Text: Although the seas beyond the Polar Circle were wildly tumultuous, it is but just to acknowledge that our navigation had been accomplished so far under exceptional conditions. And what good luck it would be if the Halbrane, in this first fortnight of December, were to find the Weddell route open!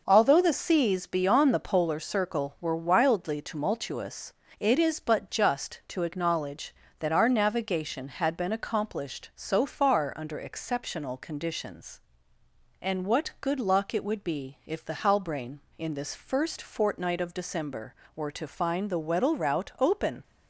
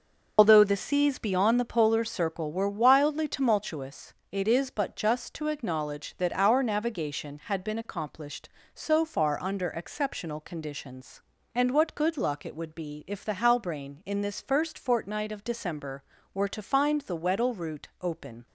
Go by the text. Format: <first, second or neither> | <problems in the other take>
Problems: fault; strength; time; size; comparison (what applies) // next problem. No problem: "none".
first | loses the start of "Although"; at 0.3 s; 95 ms